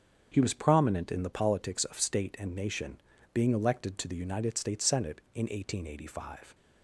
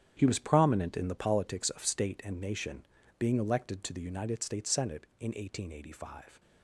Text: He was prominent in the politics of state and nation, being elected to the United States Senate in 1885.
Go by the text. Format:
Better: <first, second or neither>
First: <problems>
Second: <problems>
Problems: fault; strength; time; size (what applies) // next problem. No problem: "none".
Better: first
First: starts louder than the rest; strong; until 1.3 s; 7.5 dB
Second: gets quieter; strong; throughout; 11.5 dB // starts louder than the rest; strong; until 1.1 s; 10 dB